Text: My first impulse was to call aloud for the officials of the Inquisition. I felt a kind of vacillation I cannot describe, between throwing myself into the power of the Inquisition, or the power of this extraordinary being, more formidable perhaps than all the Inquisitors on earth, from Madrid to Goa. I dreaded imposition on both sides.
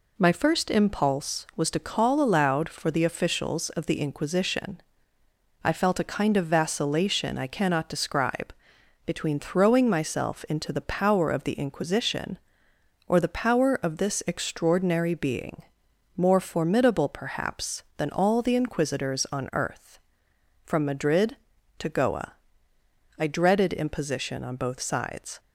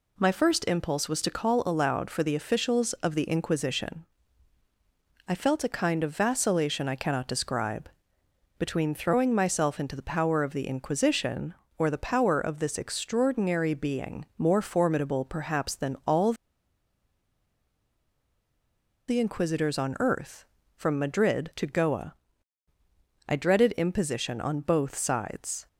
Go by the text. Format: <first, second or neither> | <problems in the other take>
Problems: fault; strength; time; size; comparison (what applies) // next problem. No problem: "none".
first | pauses between "all" and "the"; strong; at 16.3 s; 2.7 s long